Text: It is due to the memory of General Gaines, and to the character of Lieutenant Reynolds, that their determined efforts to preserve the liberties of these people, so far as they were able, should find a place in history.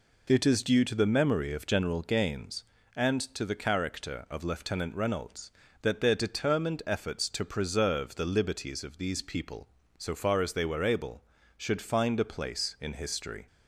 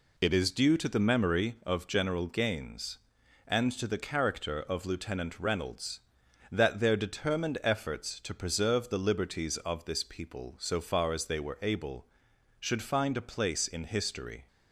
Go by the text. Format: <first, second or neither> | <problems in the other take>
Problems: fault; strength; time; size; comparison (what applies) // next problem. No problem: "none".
first | says "this" for "these"; at 9.8 s